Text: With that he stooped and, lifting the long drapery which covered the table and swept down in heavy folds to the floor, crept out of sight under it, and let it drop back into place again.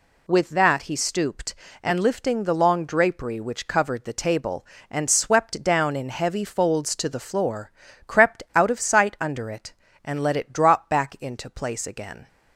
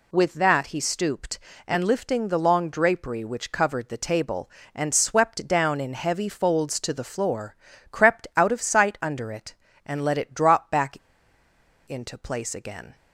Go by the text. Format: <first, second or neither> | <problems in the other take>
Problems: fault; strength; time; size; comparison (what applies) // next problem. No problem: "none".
first | pauses between "back" and "into"; noticeable; at 10.9 s; 0.90 s long